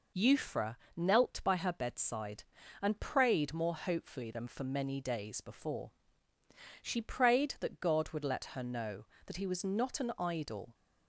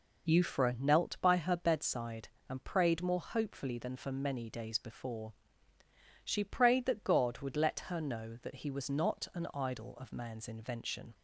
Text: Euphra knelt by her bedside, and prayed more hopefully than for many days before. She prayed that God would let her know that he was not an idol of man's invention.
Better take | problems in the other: second | pauses between "Euphra" and "knelt"; slight; at 0.7 s; 0.20 s long // stops before "of man's invention"; at 10.7 s

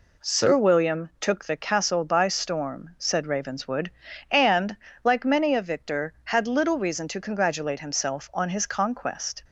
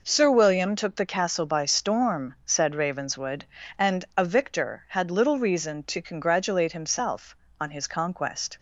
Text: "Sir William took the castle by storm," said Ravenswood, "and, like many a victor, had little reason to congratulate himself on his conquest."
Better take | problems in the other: first | skips "like many"; at 4.1 s

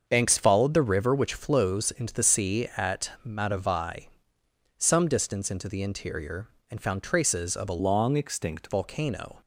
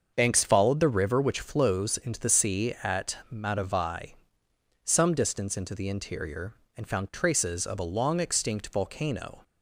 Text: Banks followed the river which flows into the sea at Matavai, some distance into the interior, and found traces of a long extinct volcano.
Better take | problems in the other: second | starts louder than the rest; until 1.0 s; 6.5 dB; also in the second // changes voice from "long" to "extinct"; from 7.7 to 8.6 s; 0.9 s long

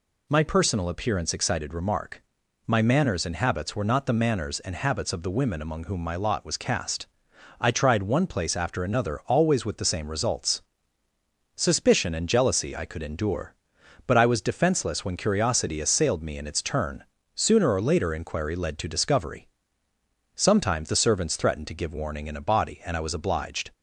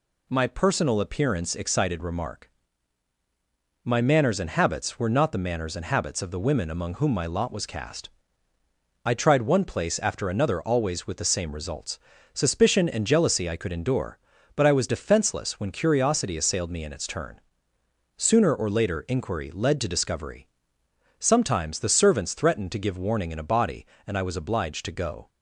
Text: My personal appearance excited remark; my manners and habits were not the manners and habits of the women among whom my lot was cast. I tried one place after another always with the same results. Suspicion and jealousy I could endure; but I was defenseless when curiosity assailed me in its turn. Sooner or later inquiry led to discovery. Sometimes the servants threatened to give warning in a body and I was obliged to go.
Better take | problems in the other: second | stops before "to go"; at 23.7 s

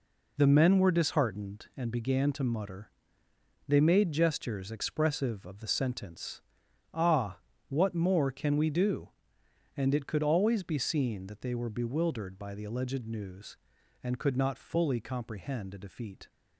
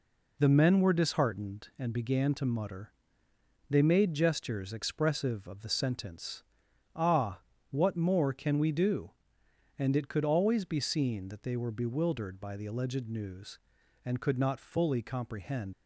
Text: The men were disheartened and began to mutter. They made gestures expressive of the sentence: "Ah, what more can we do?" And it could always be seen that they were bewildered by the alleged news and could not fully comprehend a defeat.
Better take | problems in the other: first | stops before "a defeat"; at 15.7 s

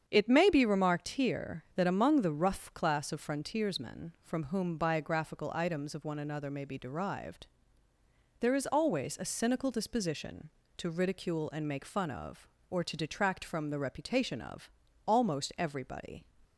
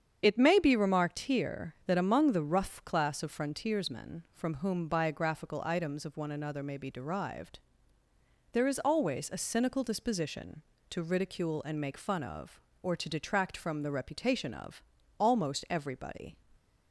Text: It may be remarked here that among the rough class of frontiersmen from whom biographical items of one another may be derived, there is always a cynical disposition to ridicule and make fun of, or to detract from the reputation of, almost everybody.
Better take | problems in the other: first | loses the start of "It"; at 0.2 s; 55 ms // starts louder than the rest; strong; until 1.2 s; 8 dB; strong in the first

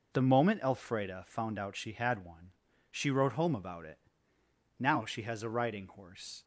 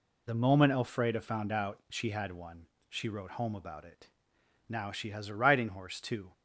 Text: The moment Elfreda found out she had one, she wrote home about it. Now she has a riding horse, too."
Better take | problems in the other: second | stops before "too"; at 6.4 s

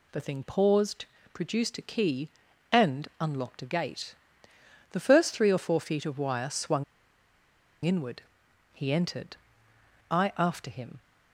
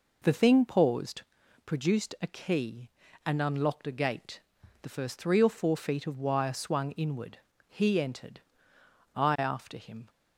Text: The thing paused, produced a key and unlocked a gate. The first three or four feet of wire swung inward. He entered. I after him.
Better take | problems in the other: second | pauses between "swung" and "inward"; at 6.8 s; 1.0 s long

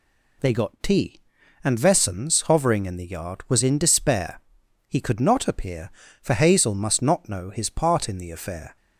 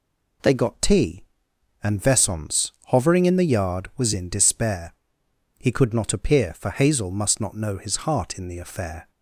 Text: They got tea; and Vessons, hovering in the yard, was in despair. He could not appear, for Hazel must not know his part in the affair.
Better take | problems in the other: first | says "heart" for "part"; at 8.0 s

